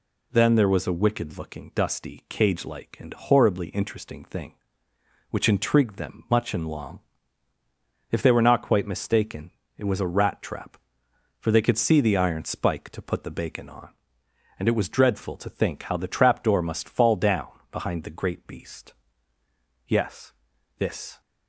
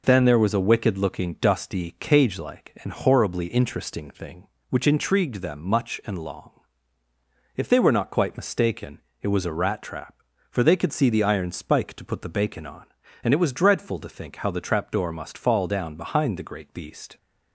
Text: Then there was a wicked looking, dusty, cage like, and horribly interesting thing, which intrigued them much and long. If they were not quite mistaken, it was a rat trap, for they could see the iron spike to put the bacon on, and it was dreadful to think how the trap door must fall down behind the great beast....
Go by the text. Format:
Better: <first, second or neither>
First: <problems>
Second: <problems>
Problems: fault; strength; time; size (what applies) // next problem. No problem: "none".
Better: second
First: pauses between "down" and "behind"; slight; at 17.4 s; 0.22 s long // goes on to say "Yes this"; from 19.8 s on; 1.3 s long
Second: none